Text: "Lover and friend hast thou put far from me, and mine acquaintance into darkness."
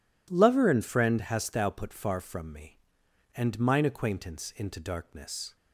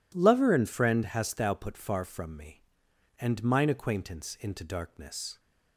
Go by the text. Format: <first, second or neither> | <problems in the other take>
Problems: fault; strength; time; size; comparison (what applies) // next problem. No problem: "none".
neither | none